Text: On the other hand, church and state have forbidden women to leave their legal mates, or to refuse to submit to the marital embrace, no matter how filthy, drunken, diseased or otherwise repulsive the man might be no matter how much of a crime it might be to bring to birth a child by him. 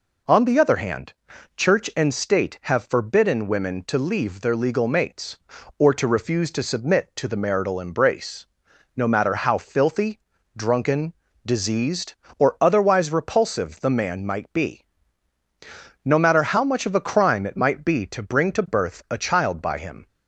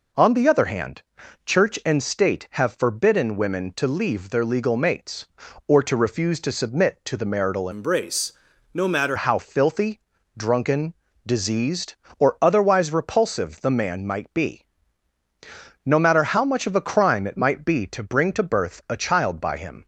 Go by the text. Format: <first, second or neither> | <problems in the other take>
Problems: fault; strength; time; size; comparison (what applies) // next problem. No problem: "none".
first | changes voice from "embrace" to "matter"; from 7.7 to 9.1 s; 1.4 s long // pauses between "be" and "no"; at 14.6 s; 1.2 s long; also in the first